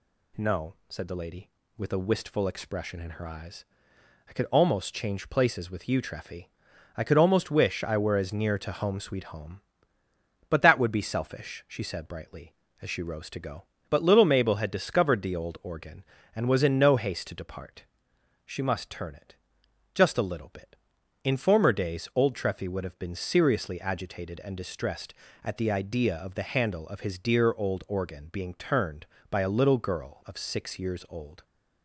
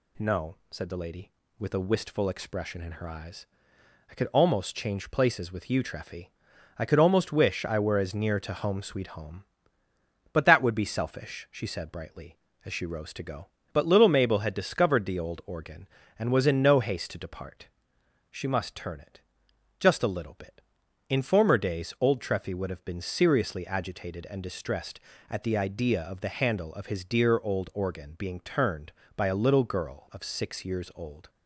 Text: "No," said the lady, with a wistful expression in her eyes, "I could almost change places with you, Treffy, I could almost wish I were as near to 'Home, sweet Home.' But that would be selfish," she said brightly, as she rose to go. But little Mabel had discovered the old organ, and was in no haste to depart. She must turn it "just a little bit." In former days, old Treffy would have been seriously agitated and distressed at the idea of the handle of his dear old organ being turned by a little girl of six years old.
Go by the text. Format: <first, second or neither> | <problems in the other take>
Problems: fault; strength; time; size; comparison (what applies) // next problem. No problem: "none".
neither | pauses between "it" and "just"; noticeable; the same in both